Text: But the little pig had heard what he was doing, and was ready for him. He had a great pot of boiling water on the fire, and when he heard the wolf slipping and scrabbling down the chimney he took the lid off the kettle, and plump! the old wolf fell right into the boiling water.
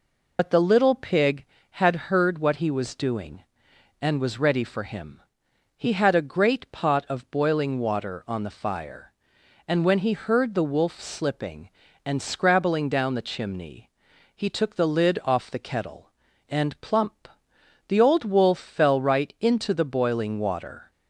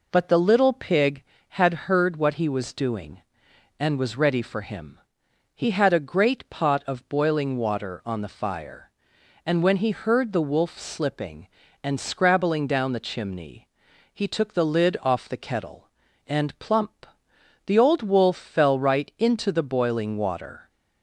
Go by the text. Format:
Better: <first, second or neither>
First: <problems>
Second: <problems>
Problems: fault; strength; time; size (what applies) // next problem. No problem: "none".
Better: second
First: loses the start of "But"; at 0.3 s; 65 ms // pauses between "chimney" and "he"; noticeable; at 13.8 s; 0.46 s long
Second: pauses between "chimney" and "he"; noticeable; at 13.6 s; 0.46 s long